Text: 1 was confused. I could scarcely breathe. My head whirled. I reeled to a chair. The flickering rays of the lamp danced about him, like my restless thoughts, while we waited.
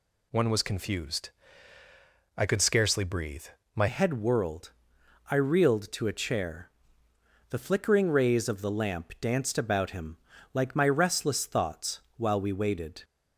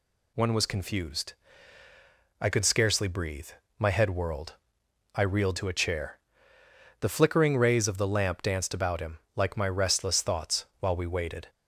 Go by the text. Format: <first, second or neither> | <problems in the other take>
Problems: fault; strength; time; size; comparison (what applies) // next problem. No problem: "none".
second | changes voice at "head"; from 3.8 s on; 9.2 s long